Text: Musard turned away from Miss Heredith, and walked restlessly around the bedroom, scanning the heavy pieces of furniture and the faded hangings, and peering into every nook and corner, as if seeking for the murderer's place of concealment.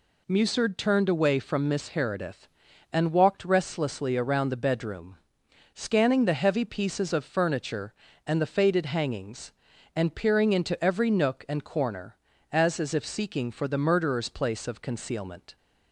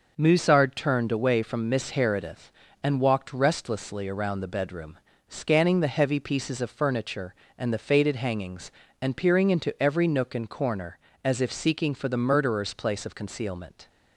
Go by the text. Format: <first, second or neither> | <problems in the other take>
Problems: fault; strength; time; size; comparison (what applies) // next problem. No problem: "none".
second | says "as" twice; at 12.7 s